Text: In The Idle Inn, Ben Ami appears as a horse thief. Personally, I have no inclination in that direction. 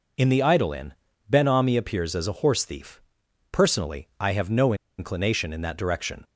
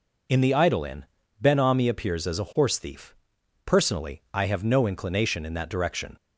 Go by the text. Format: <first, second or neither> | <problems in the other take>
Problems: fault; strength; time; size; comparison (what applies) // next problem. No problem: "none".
second | pauses between "no" and "inclination"; slight; at 4.7 s; 0.24 s long